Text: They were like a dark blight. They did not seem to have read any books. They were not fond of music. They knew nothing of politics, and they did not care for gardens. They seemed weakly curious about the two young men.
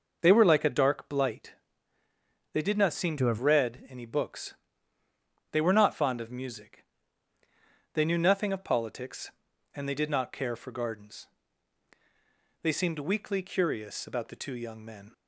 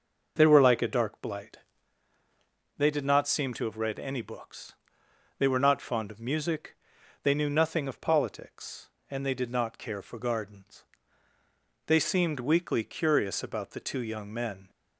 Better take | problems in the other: second | changes voice from "to" to "have"; from 3.1 to 3.3 s; 0.2 s long

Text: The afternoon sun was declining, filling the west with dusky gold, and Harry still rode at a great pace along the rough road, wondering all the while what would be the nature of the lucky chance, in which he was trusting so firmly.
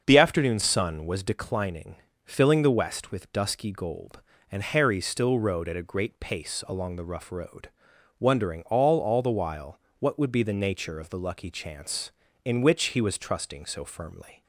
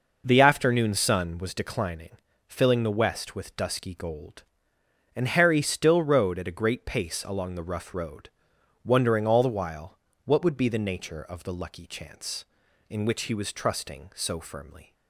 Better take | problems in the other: second | starts louder than the rest; until 1.0 s; 6.5 dB // says "all" twice; at 8.9 s // pauses between "while" and "what"; slight; at 9.7 s; 0.20 s long; slight in the second

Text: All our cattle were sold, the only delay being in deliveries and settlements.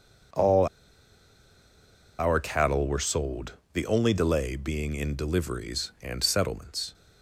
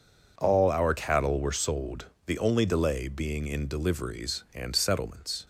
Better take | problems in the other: second | pauses between "All" and "our"; strong; at 0.6 s; 1.5 s long

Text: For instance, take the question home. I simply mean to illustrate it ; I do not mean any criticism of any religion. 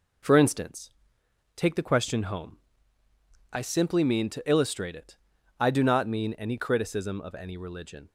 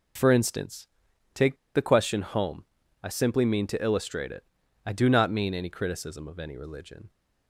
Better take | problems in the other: first | pauses between "take" and "the"; slight; at 1.5 s; 0.18 s long

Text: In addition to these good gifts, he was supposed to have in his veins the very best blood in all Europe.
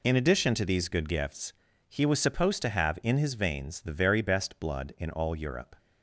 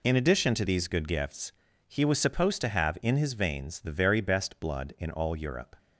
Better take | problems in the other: neither | none

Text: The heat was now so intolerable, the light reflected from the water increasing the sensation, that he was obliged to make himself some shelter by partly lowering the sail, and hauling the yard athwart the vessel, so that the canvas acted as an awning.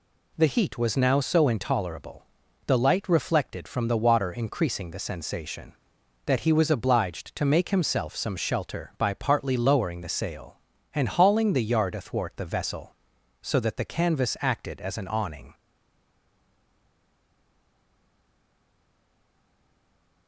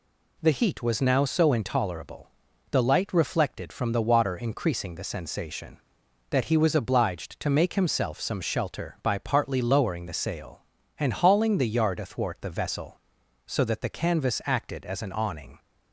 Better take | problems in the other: second | stays silent after the last word; strong; from 15.5 s on; 4.7 s long

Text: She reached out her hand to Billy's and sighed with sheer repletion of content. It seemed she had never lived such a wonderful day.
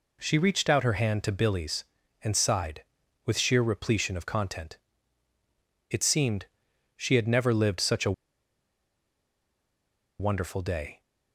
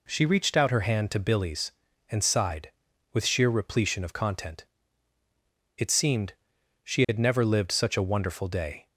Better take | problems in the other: second | pauses between "seemed" and "she"; noticeable; at 6.4 s; 0.50 s long; noticeable in the second // pauses between "a" and "wonderful"; strong; at 8.1 s; 2.0 s long

